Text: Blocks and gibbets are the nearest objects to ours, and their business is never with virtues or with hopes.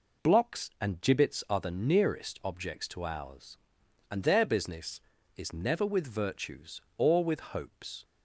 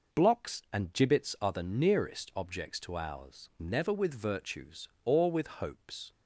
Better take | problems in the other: first | skips "and their business is"; at 3.5 s

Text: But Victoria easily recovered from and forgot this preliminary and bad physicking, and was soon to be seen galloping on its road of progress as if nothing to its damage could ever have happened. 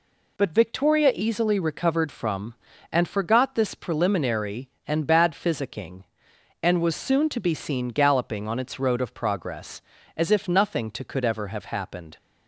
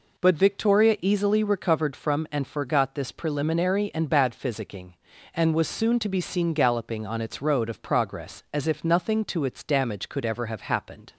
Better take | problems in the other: second | skips "its damage"; at 11.0 s

